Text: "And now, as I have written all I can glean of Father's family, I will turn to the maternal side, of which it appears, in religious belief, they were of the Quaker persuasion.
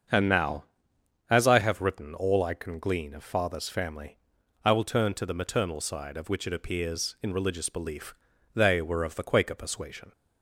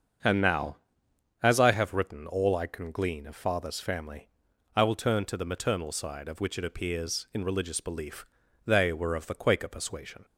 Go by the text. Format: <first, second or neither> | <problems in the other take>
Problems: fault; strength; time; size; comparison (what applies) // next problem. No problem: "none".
neither | starts louder than the rest; the same in both